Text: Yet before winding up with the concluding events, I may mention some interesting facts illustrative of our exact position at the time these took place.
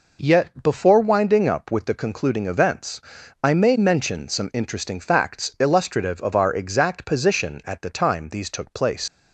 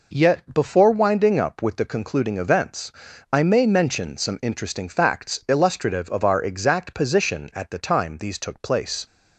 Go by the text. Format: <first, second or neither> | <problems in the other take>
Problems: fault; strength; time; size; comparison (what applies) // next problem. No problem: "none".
second | leaves "place" unfinished; at 9.0 s; 85 ms